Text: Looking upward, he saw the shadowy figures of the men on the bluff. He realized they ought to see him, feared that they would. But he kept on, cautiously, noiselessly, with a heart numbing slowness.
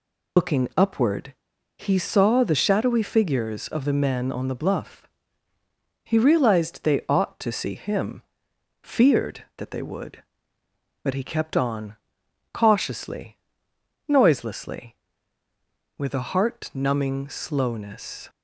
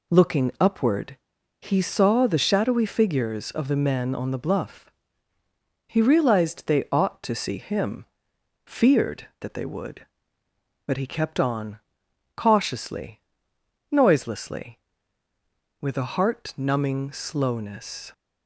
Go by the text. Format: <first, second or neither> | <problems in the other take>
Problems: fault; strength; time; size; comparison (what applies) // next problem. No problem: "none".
second | loses the start of "Looking"; at 0.3 s; 90 ms